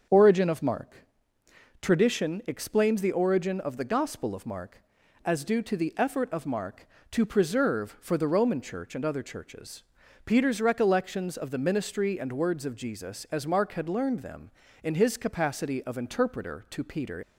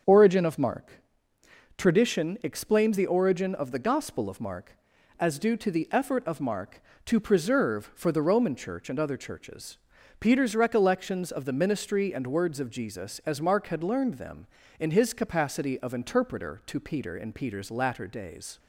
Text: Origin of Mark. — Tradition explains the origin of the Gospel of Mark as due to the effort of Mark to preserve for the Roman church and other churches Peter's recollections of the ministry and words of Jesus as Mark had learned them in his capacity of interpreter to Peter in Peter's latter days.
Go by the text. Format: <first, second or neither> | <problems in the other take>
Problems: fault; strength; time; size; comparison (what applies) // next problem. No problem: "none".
second | starts louder than the rest; until 1.8 s; 6.5 dB; also in the second // pauses between "churches" and "Peter's"; at 9.8 s; 0.42 s long; also in the second // stops before "in Peter's latter days"; at 17.2 s